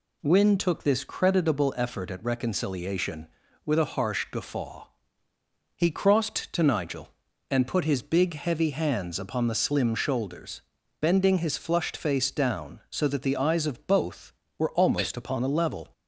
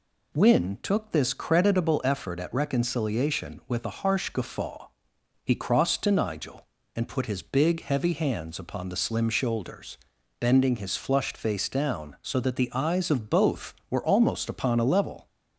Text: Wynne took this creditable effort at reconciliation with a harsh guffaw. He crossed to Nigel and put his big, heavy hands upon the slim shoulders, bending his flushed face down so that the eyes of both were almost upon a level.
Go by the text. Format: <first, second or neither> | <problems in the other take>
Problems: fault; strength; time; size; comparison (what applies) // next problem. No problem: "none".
neither | none